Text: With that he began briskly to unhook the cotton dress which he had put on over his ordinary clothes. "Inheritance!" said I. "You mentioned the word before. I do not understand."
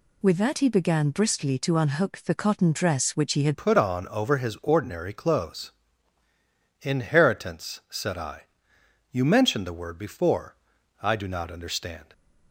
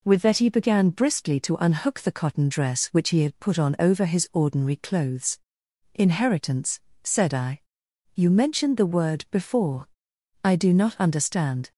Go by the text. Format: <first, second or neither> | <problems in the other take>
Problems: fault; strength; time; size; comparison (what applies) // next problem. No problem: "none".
second | changes voice at "put"; from 3.5 s on; 8.6 s long